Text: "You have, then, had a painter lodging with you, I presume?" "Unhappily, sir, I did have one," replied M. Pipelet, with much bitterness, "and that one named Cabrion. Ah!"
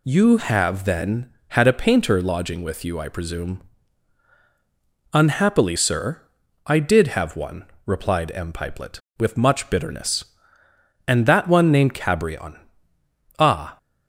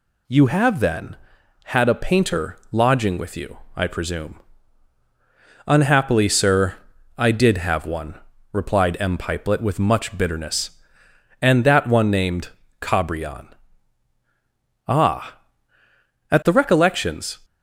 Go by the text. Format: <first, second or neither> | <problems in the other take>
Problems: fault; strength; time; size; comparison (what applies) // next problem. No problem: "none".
first | pauses between "named" and "Cabrion"; slight; at 12.4 s; 0.30 s long // goes on to say "At the recollections"; noticeable; from 16.3 s on; 1.0 s long